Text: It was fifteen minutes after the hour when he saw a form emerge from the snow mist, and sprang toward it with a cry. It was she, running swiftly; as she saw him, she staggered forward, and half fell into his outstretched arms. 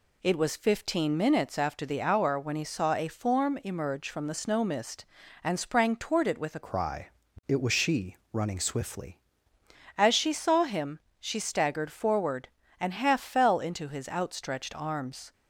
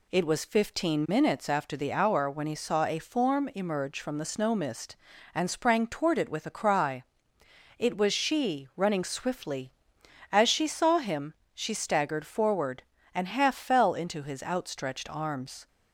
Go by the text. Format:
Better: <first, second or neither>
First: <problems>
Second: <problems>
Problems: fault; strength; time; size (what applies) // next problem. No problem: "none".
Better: second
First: changes voice from "cry" to "swiftly"; from 6.6 to 9.1 s; 2.5 s long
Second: none